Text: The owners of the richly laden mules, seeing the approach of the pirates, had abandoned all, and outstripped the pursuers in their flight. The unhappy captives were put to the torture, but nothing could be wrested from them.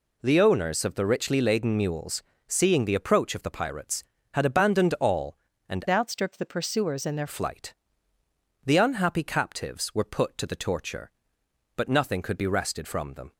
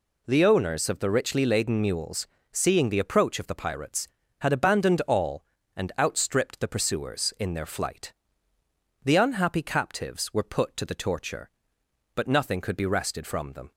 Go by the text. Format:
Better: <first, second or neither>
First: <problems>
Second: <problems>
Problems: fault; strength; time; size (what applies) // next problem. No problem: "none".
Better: second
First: changes voice from "outstripped" to "their"; from 5.8 to 7.2 s; 1.4 s long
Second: none